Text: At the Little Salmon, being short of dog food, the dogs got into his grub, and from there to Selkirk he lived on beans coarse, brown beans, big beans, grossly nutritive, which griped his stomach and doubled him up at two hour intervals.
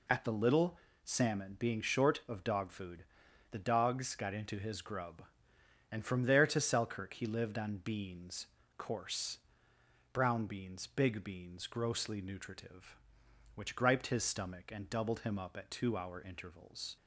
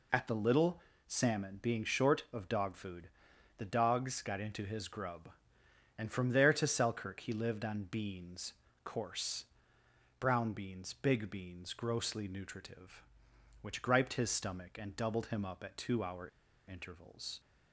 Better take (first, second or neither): first